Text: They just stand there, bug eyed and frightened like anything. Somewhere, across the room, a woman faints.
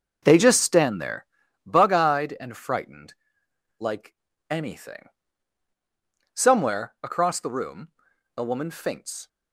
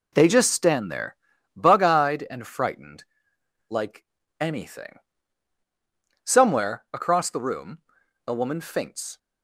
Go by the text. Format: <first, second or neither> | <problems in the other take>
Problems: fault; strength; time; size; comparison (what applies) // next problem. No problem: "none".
second | starts louder than the rest; noticeable; until 1.1 s; 6 dB // pauses between "frightened" and "like"; noticeable; at 3.1 s; 0.64 s long; noticeable in the second // pauses between "like" and "anything"; slight; at 4.1 s; 0.34 s long; slight in the second